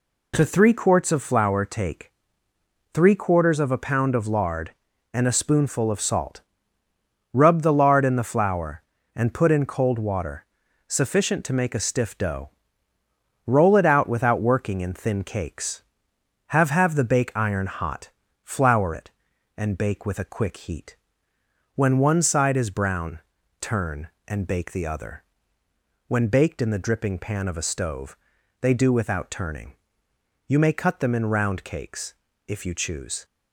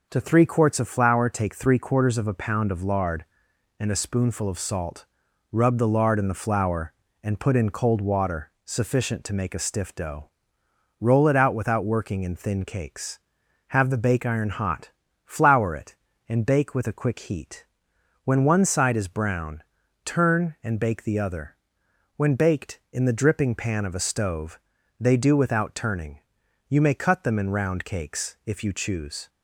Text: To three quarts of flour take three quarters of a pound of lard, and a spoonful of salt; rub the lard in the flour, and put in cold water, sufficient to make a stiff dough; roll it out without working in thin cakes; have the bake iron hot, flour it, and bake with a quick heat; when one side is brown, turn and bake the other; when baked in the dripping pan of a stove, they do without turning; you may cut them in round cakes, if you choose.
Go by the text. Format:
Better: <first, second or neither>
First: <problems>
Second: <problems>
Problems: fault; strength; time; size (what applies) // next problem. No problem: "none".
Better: second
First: pauses between "take" and "three"; noticeable; at 2.1 s; 0.82 s long // says "have" twice; at 16.6 s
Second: none